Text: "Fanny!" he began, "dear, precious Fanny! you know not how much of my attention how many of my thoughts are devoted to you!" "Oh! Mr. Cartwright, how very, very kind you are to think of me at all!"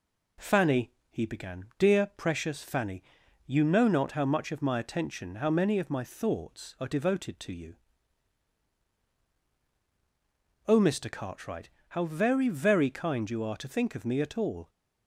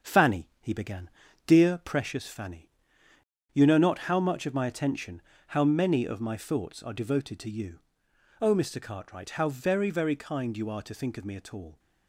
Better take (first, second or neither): first